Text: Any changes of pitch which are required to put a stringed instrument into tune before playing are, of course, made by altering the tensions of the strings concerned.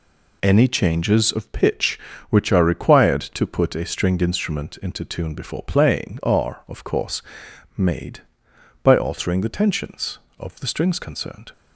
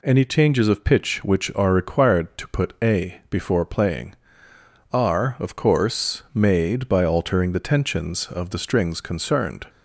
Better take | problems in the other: first | skips "stringed instrument into tune"; at 3.2 s

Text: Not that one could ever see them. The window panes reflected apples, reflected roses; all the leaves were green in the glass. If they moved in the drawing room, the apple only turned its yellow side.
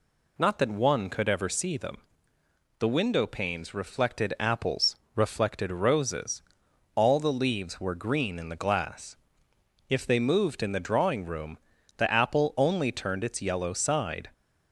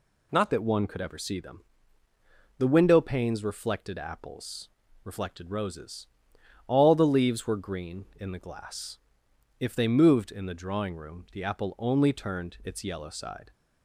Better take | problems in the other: first | changes voice at "that"; from 0.5 s on; 13.0 s long

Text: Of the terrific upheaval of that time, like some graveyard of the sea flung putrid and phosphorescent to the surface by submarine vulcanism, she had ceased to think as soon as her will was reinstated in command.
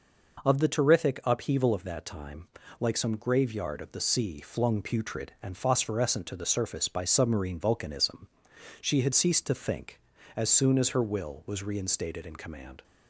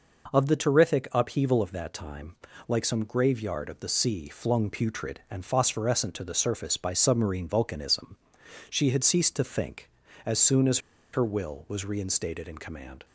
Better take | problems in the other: first | pauses between "as" and "her"; slight; at 10.7 s; 0.34 s long

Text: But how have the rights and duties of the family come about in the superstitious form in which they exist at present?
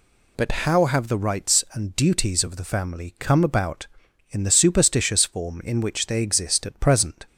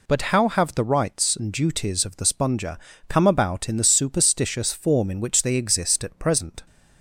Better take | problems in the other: first | says "sponger" for "family"; at 2.2 s

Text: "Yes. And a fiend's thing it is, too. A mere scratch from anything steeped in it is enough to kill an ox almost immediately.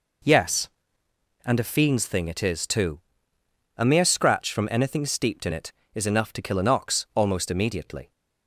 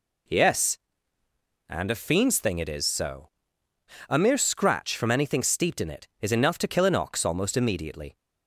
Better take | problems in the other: first | says "so" for "too"; at 2.8 s

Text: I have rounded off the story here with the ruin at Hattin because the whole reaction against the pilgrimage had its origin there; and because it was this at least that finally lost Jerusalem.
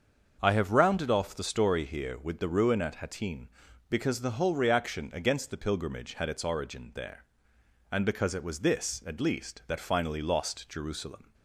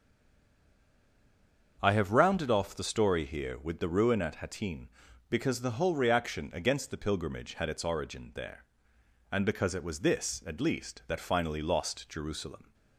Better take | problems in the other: first | stays silent before the first word; noticeable; until 1.7 s; 1.7 s long // starts louder than the rest; until 2.8 s; 6.5 dB; also in the first

